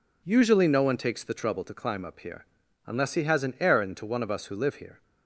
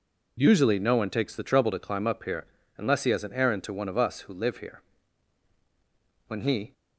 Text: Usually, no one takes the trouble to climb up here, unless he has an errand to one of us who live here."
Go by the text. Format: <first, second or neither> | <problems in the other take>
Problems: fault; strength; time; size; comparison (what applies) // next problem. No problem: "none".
first | goes on to say "When he"; slight; from 6.2 s on; 0.44 s long